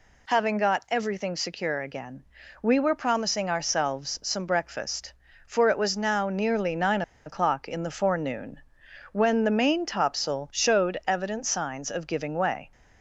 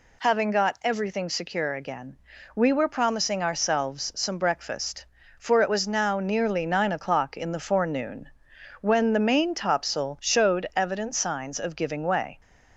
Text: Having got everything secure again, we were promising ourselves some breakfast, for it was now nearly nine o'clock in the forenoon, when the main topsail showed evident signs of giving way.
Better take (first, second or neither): second